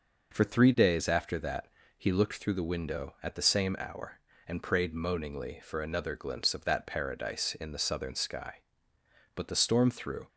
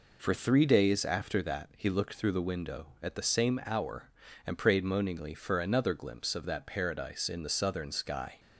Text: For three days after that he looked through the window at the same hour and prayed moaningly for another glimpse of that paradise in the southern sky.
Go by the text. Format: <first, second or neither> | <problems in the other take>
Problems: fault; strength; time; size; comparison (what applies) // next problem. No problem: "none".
second | pauses between "that" and "he"; slight; at 1.6 s; 0.28 s long // goes on to say "But the storm through"; noticeable; from 9.3 s on; 0.92 s long